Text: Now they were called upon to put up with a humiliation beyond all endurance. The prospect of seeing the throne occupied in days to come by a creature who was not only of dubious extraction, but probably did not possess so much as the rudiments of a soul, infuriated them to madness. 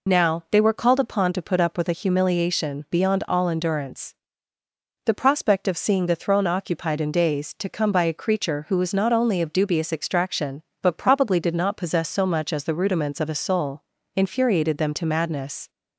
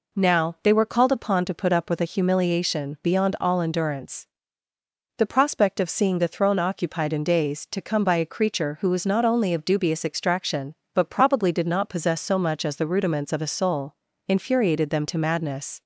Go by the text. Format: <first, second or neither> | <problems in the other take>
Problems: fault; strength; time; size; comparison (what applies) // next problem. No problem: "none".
second | loses the start of "Now"; at 0.0 s; 45 ms